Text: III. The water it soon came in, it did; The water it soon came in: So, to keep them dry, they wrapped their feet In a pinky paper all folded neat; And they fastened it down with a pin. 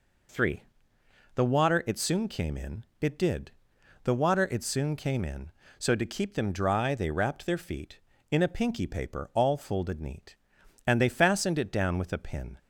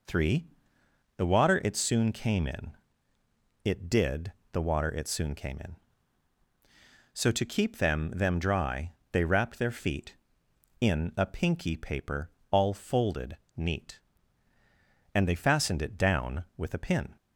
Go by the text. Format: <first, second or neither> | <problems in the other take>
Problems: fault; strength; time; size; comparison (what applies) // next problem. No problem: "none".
first | says "them" twice; at 8.1 s // pauses between "paper" and "all"; slight; at 12.2 s; 0.22 s long // pauses between "folded" and "neat"; slight; at 13.3 s; 0.20 s long